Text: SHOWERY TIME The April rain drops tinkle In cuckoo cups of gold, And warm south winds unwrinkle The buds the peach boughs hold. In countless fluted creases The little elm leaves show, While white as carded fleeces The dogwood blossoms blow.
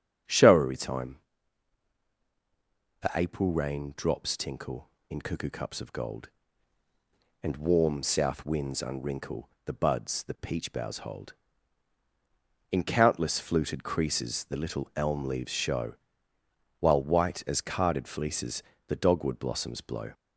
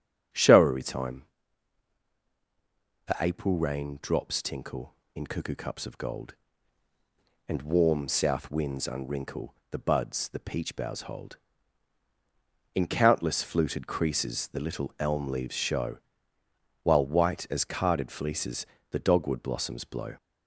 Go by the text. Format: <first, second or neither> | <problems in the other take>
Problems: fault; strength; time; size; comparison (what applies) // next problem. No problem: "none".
neither | starts louder than the rest; strong; the same in both // pauses between "TIME" and "The"; strong; the same in both // pauses between "unwrinkle" and "The"; slight; the same in both // pauses between "fleeces" and "The"; slight; the same in both